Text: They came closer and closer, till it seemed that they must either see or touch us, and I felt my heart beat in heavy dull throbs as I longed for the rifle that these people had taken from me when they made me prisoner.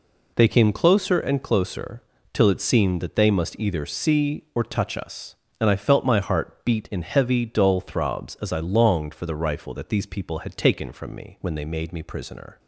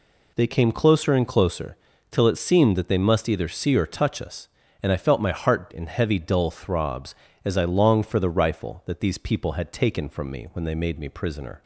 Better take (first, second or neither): first